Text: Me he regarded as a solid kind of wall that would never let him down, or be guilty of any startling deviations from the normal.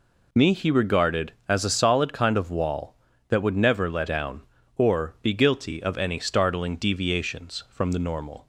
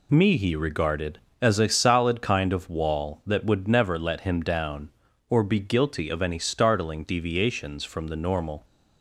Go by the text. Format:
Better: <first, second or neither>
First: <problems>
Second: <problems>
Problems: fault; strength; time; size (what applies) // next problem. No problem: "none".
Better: second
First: skips "him"; at 4.0 s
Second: none